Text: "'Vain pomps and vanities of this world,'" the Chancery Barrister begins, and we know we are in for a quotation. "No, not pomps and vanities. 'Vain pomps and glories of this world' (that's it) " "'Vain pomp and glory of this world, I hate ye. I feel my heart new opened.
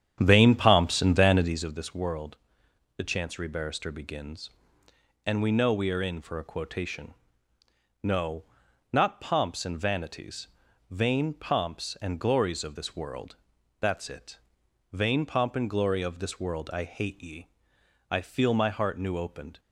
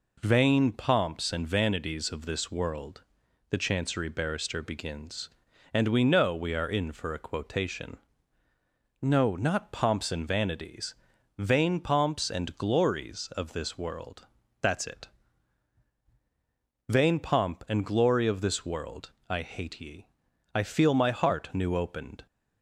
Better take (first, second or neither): second